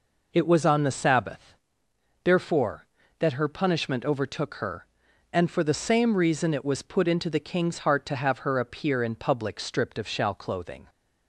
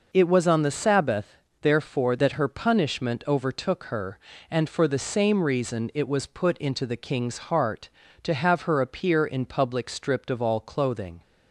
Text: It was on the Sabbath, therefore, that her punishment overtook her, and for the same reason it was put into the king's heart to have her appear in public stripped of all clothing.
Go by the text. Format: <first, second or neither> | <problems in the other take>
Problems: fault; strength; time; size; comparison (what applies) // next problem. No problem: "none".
second | says "shall" for "all"; at 10.0 s